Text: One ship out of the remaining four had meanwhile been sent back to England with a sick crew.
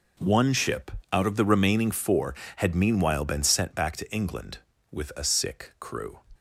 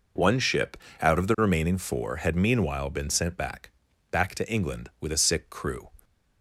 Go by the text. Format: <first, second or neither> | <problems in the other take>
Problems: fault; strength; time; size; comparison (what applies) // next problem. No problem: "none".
first | pauses between "ship" and "out"; slight; at 0.7 s; 0.20 s long; slight in the first // says "back" twice; at 4.1 s